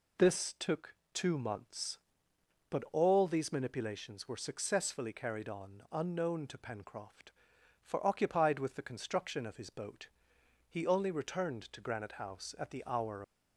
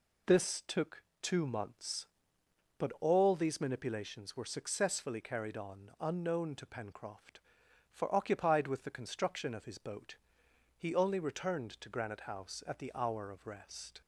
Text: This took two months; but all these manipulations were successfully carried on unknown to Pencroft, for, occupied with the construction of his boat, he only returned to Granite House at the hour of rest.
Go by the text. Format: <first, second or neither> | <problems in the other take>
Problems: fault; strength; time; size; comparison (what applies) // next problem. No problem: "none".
second | pauses between "took" and "two"; slight; at 0.9 s; 0.18 s long; slight in the second // stops before "of rest"; at 13.2 s